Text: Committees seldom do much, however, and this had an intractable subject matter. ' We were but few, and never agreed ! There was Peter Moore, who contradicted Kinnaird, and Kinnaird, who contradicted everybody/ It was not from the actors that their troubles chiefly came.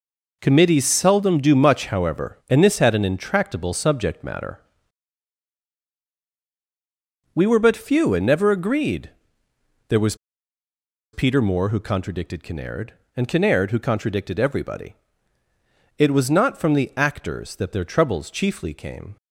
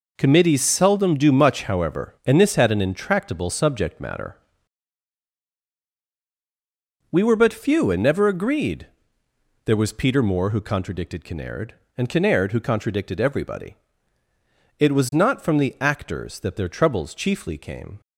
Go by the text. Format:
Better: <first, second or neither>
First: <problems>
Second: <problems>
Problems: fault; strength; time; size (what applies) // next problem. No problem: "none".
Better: second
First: pauses between "was" and "Peter"; at 10.1 s; 0.98 s long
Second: none